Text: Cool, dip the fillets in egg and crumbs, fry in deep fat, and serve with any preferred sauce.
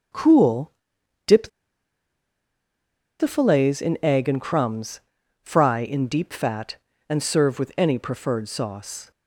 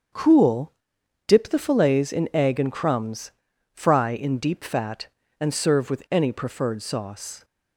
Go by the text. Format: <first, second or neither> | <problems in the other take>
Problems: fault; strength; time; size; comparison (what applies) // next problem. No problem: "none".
second | starts louder than the rest; until 3.4 s; 7 dB; also in the second // pauses between "dip" and "the"; strong; at 1.4 s; 1.7 s long